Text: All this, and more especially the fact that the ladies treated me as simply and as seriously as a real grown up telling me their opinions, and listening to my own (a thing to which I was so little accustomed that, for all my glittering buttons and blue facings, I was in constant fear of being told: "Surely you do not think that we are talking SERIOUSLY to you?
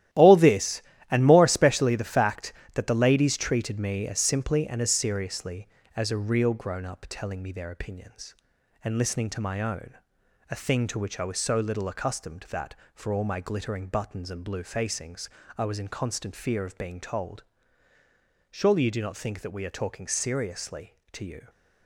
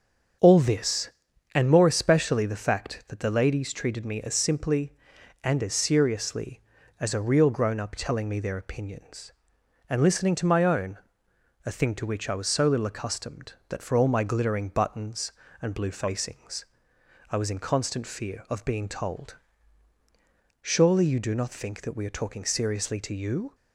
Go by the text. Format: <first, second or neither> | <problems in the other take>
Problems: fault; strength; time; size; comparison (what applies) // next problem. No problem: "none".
second | gets quieter; strong; throughout; 10.5 dB // starts louder than the rest; strong; until 1.4 s; 13 dB; strong in the second